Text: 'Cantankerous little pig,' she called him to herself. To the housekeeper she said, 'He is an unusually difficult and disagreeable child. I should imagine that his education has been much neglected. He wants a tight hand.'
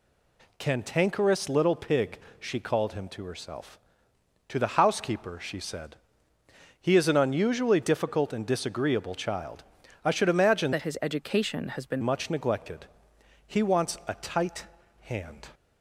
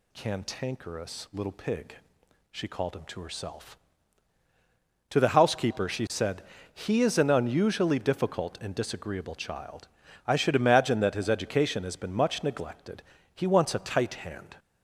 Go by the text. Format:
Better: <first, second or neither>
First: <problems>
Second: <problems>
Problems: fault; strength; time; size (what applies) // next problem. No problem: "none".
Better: second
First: changes voice from "that" to "been"; from 10.7 to 12.0 s; 1.3 s long // pauses between "tight" and "hand"; slight; at 14.6 s; 0.34 s long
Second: none